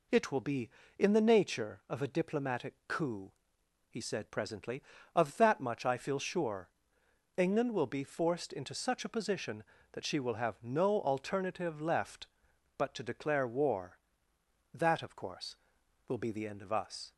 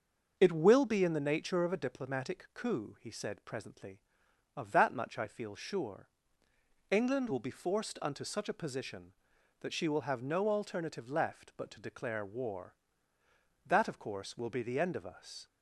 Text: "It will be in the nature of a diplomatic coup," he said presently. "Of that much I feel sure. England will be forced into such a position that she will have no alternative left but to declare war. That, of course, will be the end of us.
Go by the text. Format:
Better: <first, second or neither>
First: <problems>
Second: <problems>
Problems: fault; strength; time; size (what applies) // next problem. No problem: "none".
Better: first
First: none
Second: starts louder than the rest; until 1.3 s; 6 dB // says "unto" for "into"; at 8.0 s